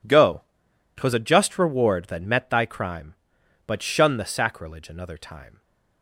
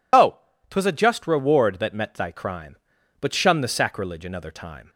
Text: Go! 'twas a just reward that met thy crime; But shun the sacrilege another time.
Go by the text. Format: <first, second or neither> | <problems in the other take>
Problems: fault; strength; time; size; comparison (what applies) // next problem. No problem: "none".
first | loses the start of "Go"; at 0.1 s; 80 ms